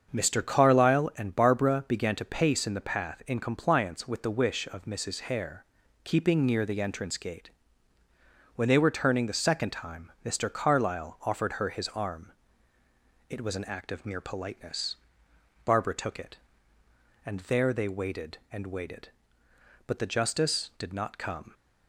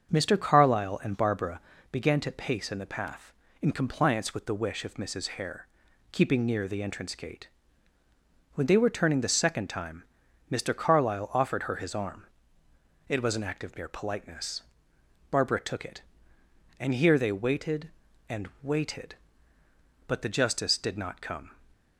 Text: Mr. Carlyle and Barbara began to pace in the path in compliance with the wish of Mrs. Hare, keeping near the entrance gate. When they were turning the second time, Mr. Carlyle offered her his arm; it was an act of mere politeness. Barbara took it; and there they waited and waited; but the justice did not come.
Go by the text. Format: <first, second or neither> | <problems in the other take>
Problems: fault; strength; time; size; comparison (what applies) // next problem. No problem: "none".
first | starts louder than the rest; until 1.1 s; 7 dB; also in the first // pauses between "Barbara" and "began"; slight; at 1.5 s; 0.32 s long // says "here" for "there"; at 16.9 s // pauses between "and" and "waited"; slight; at 18.4 s; 0.16 s long